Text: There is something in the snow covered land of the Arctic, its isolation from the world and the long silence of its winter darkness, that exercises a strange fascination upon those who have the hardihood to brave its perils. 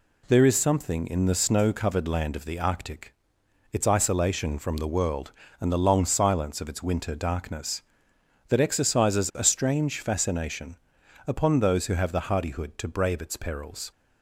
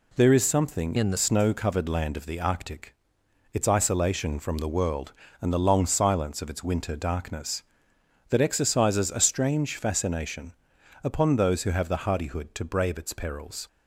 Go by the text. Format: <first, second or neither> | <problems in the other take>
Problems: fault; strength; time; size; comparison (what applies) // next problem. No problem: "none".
first | changes voice from "in" to "the"; from 0.9 to 1.1 s; 0.2 s long // pauses between "fascination" and "upon"; noticeable; at 10.5 s; 0.50 s long; noticeable in the first